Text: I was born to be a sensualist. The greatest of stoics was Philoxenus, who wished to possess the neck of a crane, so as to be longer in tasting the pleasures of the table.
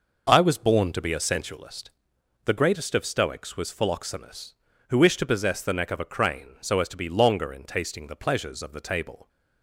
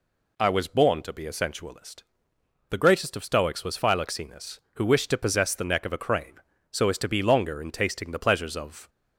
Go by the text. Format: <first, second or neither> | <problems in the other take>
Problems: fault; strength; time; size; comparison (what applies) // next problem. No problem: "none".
first | stops before "the table"; at 8.8 s